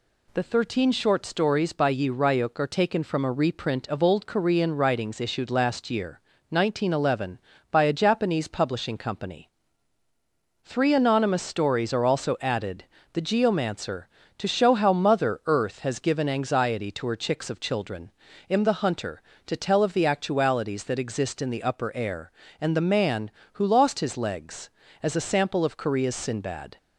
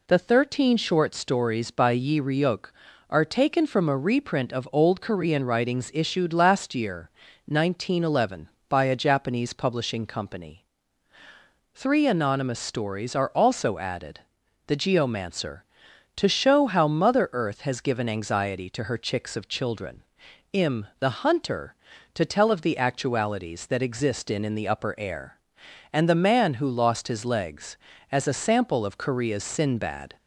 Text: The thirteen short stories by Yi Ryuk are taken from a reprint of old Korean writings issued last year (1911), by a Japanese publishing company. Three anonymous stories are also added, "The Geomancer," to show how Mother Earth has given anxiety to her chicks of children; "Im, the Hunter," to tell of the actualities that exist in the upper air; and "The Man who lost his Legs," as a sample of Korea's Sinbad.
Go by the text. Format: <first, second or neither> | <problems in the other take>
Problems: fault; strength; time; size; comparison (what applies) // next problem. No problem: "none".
first | says "in" twice; at 24.4 s